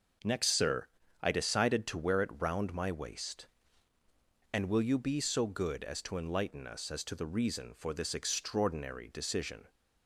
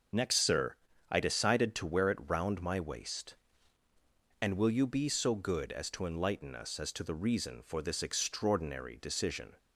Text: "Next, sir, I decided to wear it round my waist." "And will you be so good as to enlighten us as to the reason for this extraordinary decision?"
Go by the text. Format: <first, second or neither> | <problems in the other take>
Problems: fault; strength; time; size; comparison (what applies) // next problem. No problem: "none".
first | loses the start of "Next"; at 0.1 s; 35 ms // starts louder than the rest; noticeable; until 1.4 s; 6 dB; noticeable in the first